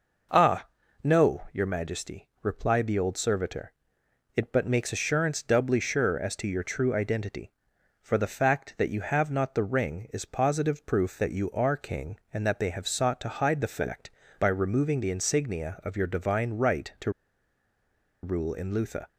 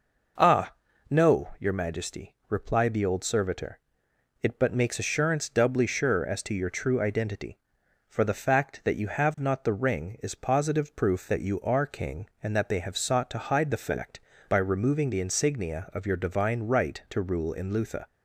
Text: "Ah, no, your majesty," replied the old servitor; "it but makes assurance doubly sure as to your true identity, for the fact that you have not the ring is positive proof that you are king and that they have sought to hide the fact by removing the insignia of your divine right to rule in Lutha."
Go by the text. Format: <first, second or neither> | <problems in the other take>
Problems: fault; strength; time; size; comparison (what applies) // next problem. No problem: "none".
second | pauses between "to" and "rule"; at 17.1 s; 1.1 s long